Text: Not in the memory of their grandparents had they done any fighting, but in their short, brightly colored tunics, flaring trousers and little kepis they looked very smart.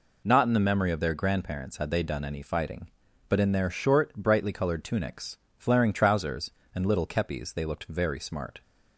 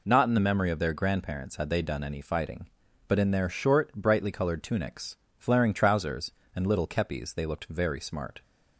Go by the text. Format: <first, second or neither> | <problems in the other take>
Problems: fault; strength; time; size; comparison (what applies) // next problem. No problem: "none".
neither | none